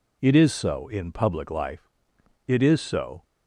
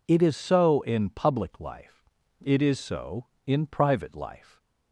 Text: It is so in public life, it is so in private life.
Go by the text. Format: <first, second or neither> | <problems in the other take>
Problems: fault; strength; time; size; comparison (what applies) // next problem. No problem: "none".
second | stops before "in private life"; at 3.2 s